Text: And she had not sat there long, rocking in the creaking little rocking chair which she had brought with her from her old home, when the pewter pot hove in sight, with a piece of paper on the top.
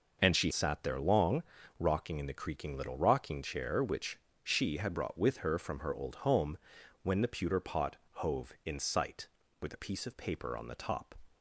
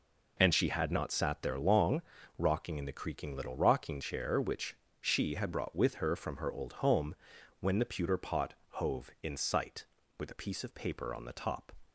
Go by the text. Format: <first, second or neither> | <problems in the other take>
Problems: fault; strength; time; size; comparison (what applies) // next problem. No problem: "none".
second | skips "had not"; at 0.5 s // pauses between "which" and "she"; slight; at 4.1 s; 0.24 s long; slight in the second // pauses between "pot" and "hove"; slight; at 7.9 s; 0.18 s long; slight in the second